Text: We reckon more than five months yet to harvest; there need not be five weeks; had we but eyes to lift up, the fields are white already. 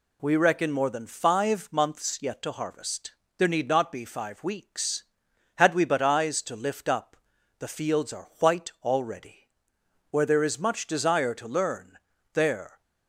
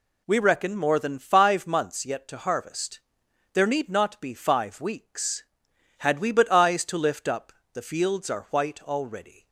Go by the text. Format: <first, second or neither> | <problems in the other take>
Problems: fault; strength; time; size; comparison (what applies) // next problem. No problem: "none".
second | goes on to say "Where there is much desire to learn there"; strong; from 10.1 s on; 2.7 s long